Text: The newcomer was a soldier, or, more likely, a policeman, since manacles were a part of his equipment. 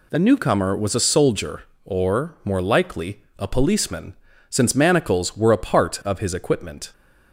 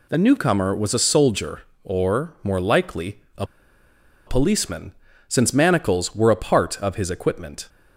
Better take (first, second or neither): first